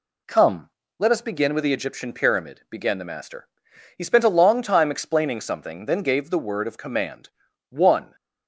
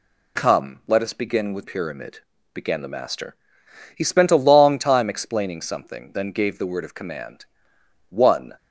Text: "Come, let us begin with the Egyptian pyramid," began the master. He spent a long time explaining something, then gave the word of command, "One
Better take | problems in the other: first | skips "the Egyptian"; at 1.6 s

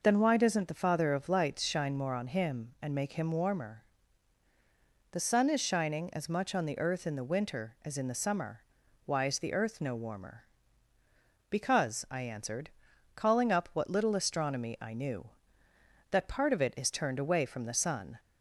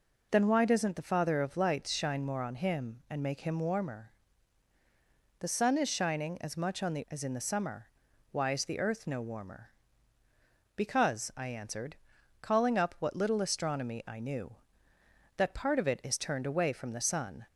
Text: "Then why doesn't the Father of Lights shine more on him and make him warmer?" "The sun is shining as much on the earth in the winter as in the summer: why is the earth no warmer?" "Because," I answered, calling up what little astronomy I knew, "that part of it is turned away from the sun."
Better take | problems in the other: first | skips "earth in the winter"; at 7.0 s

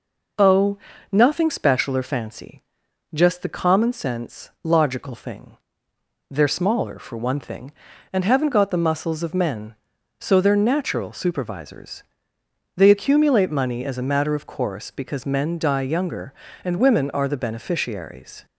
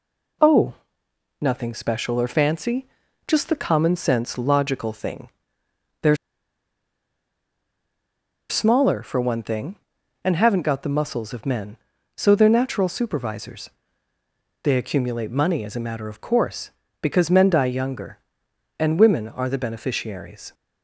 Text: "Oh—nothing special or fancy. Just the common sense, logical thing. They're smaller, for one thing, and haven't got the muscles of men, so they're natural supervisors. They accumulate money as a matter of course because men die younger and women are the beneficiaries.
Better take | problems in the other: first | pauses between "They're" and "smaller"; strong; at 6.1 s; 2.3 s long

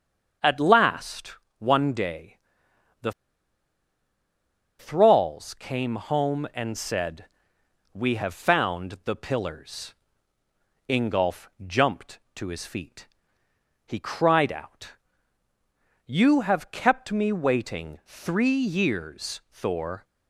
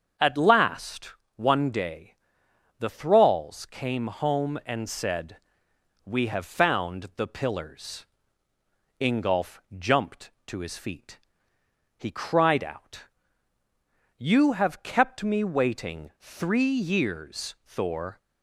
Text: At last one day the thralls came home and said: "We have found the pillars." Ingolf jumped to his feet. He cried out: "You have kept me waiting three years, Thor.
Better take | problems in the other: second | starts louder than the rest; until 1.6 s; 7 dB; also in the second // pauses between "last" and "one"; slight; at 1.3 s; 0.24 s long; slight in the second // pauses between "day" and "the"; noticeable; at 2.3 s; 0.64 s long; noticeable in the second // pauses between "the" and "thralls"; strong; at 3.1 s; 1.6 s long // pauses between "Ingolf" and "jumped"; slight; at 11.4 s; 0.18 s long; slight in the second

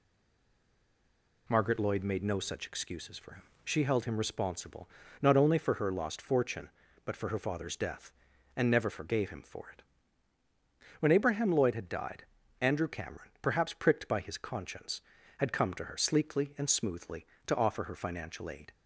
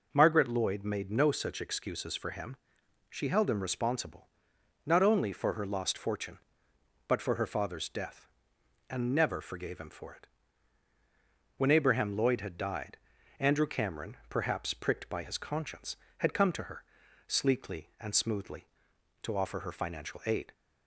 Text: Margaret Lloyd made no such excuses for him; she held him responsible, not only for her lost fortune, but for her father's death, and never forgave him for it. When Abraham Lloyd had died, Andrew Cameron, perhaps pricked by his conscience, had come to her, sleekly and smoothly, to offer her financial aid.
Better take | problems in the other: second | stays silent before the first word; noticeable; until 1.4 s; 1.4 s long

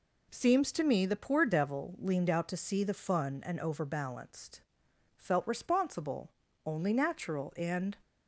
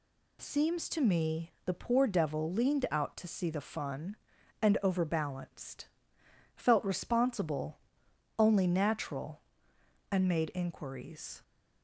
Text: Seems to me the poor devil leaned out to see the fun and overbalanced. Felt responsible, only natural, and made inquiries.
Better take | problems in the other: second | stops before "made inquiries"; at 8.0 s

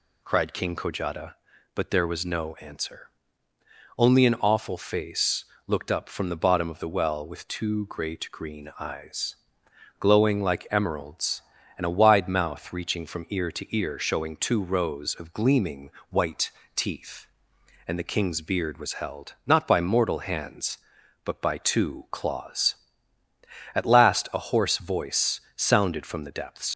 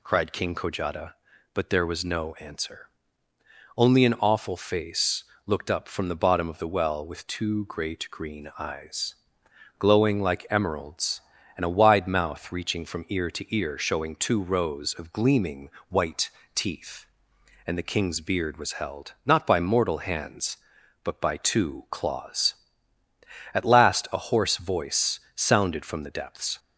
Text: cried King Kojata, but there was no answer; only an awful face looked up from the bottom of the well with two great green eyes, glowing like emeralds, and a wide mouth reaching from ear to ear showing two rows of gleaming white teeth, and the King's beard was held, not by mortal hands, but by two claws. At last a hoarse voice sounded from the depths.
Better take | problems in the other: second | pauses between "face" and "looked"; slight; at 5.4 s; 0.24 s long; slight in the second // pauses between "gleaming" and "white"; slight; at 15.8 s; 0.20 s long; slight in the second // pauses between "white" and "teeth"; slight; at 16.5 s; 0.22 s long; slight in the second // pauses between "voice" and "sounded"; slight; at 25.4 s; 0.16 s long; slight in the second // leaves "depths" unfinished; at 26.7 s; 55 ms

